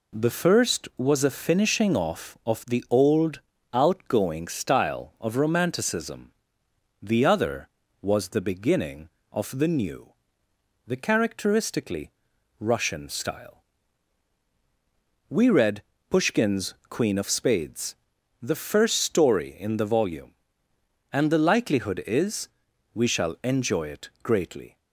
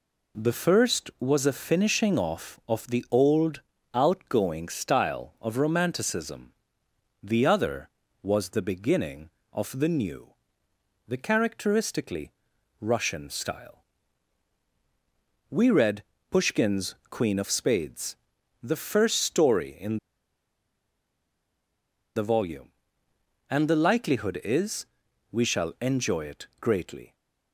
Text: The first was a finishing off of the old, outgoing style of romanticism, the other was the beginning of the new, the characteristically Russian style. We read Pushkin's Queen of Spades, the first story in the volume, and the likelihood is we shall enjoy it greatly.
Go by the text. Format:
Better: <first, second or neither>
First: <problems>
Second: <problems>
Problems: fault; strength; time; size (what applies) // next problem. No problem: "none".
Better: first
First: pauses between "characteristically" and "Russian"; noticeable; at 12.1 s; 0.50 s long // pauses between "read" and "Pushkin's"; slight; at 15.8 s; 0.28 s long // pauses between "is" and "we"; noticeable; at 22.4 s; 0.46 s long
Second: pauses between "characteristically" and "Russian"; noticeable; at 12.3 s; 0.50 s long // pauses between "read" and "Pushkin's"; slight; at 16.0 s; 0.28 s long // pauses between "in" and "the"; strong; at 19.9 s; 2.1 s long // pauses between "is" and "we"; noticeable; at 24.8 s; 0.46 s long